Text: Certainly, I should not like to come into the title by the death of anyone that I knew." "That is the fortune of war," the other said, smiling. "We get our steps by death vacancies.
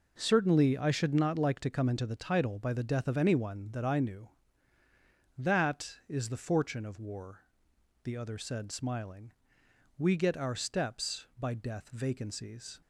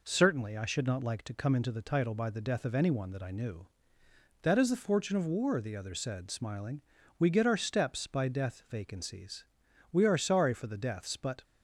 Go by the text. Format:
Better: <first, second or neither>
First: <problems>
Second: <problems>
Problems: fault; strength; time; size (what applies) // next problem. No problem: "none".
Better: first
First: none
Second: goes on to say "We are sorry for the deaths but"; from 9.9 s on; 1.5 s long